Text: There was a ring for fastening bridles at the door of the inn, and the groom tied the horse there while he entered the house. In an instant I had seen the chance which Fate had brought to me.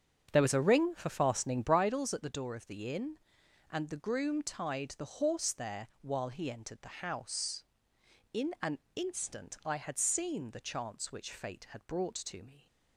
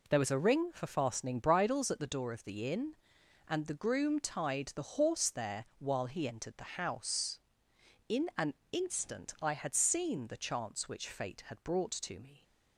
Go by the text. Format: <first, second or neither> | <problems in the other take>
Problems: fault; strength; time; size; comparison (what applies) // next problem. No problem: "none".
second | starts louder than the rest; strong; until 1.8 s; 7.5 dB // pauses between "an" and "instant"; slight; at 8.7 s; 0.16 s long; slight in the second